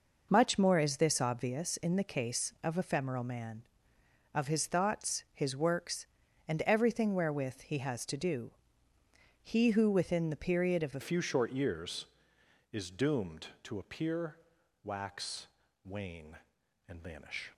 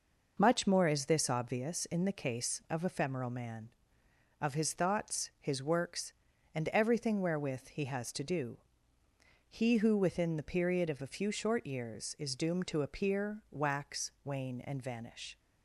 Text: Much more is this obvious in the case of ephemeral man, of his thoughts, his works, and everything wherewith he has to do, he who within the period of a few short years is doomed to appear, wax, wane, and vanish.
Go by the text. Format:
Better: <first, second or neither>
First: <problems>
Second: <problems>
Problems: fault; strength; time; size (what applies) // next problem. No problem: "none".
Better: second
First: changes voice at "few"; from 11.0 s on; 6.5 s long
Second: none